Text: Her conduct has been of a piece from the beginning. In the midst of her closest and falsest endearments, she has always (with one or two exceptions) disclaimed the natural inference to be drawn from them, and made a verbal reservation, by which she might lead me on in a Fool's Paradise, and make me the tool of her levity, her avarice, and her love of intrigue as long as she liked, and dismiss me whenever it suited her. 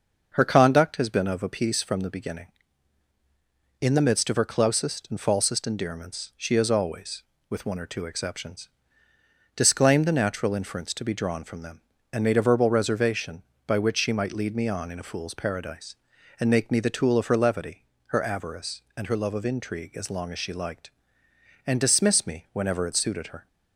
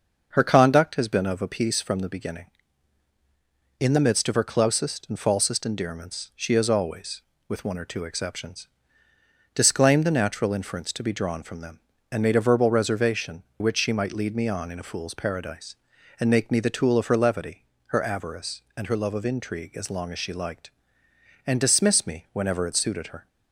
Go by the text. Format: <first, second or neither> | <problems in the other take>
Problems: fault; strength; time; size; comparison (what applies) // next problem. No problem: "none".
first | starts louder than the rest; until 1.3 s; 6.5 dB; also in the first // skips "by"; at 13.5 s